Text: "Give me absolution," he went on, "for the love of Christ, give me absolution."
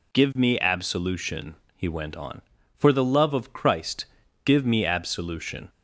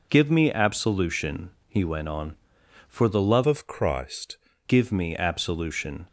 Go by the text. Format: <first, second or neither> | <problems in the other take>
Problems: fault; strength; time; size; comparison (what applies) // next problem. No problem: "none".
first | changes voice from "of" to "Christ"; from 3.4 to 4.3 s; 0.9 s long